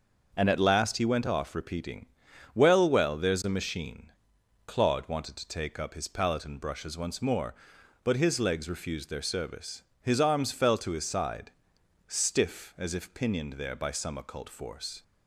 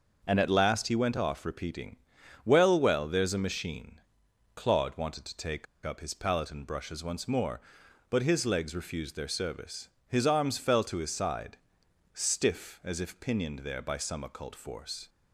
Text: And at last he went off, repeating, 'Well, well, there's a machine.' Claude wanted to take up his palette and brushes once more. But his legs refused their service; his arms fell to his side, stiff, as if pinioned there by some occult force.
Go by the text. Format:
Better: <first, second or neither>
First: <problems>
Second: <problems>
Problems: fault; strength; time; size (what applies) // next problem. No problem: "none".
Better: first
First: starts louder than the rest; until 1.3 s; 6.5 dB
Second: starts louder than the rest; until 1.2 s; 6 dB // pauses between "take" and "up"; slight; at 5.6 s; 0.19 s long